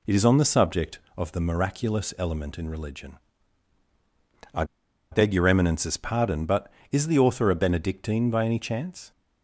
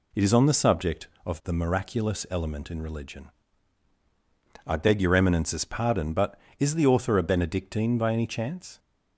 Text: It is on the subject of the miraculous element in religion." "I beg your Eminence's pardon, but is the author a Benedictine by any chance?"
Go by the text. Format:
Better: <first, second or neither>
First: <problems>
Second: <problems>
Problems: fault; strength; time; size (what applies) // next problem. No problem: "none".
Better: second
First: pauses between "I" and "beg"; noticeable; at 4.6 s; 0.47 s long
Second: none